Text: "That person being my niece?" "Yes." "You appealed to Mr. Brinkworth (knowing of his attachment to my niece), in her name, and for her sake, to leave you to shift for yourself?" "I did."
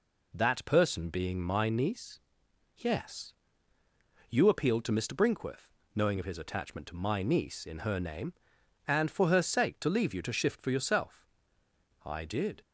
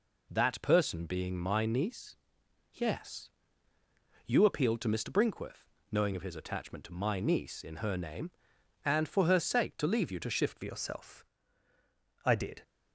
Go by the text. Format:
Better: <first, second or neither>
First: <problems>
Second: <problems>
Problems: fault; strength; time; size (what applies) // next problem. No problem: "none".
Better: first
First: none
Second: changes voice at "yourself"; from 10.6 s on; 2.0 s long